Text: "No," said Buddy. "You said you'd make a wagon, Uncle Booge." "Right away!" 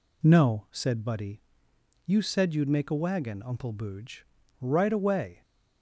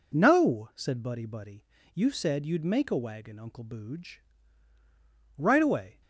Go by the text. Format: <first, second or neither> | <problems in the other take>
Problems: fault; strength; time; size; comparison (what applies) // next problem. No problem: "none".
first | says "Buddy" twice; at 1.2 s